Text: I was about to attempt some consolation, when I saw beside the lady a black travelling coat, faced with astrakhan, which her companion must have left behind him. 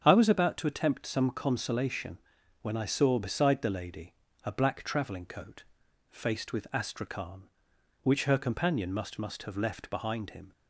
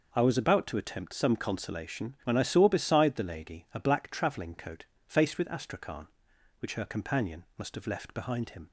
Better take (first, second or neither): second